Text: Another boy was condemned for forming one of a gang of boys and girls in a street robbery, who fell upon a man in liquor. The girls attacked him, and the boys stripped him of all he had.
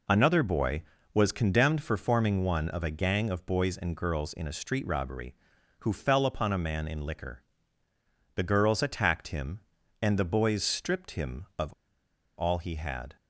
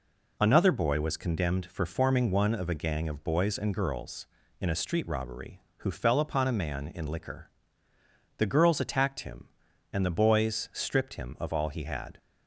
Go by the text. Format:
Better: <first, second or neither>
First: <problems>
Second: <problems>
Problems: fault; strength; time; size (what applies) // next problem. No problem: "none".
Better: second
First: pauses between "of" and "all"; noticeable; at 11.7 s; 0.64 s long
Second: none